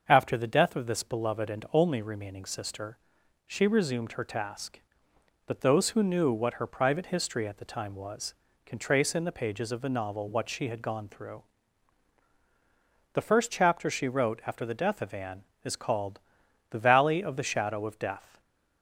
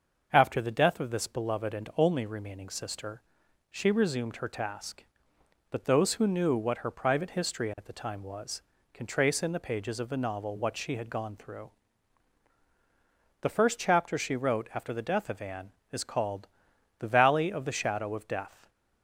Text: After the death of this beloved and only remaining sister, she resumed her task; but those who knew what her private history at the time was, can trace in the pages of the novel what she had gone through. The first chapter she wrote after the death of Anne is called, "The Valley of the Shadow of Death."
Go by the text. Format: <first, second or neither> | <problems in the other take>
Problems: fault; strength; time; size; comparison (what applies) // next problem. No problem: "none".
neither | starts louder than the rest; the same in both